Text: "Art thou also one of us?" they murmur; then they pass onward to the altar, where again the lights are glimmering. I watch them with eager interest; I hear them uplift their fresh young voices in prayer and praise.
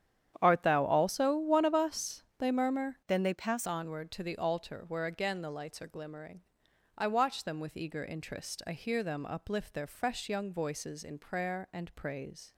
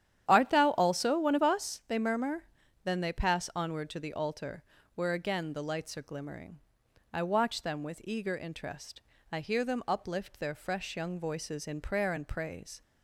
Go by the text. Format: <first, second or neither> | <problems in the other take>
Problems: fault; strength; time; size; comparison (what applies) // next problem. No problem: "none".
second | starts louder than the rest; strong; until 1.4 s; 9.5 dB; strong in the second // changes voice from "then" to "pass"; from 3.0 to 3.6 s; 0.6 s long